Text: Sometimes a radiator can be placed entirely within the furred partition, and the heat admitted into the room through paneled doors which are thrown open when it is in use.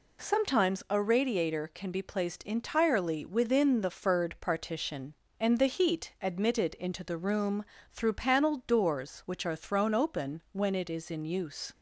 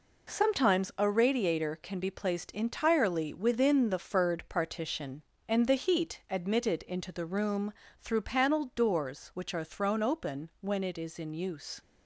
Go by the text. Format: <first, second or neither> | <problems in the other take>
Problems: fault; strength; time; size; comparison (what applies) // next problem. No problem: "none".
first | gets quieter; throughout; 7 dB // pauses between "room" and "through"; slight; at 7.7 s; 0.26 s long; slight in the first